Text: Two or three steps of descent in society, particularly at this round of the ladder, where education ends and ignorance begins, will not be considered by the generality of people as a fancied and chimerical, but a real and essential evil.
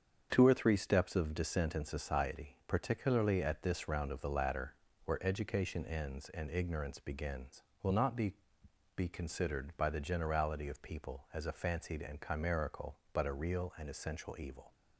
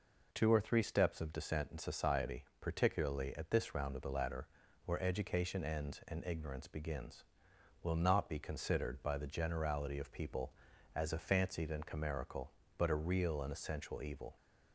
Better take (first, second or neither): second